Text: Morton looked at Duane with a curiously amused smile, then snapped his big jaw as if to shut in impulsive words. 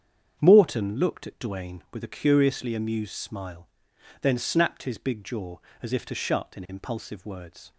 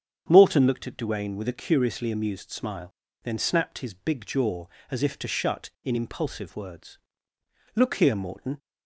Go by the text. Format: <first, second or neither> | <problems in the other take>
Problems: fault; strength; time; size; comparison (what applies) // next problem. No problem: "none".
first | starts louder than the rest; strong; until 1.2 s; 7.5 dB; strong in the first // goes on to say "Look here Morton"; noticeable; from 7.7 s on; 0.82 s long